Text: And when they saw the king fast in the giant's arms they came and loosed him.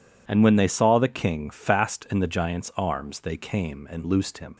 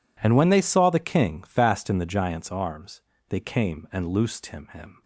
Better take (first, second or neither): first